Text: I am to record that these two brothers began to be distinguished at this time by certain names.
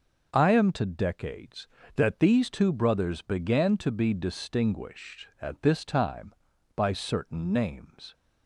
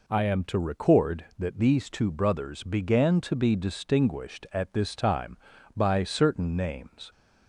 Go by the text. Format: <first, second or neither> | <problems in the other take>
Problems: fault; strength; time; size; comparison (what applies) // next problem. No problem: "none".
second | starts louder than the rest; noticeable; until 1.3 s; 6 dB // says "decades" for "record"; at 0.8 s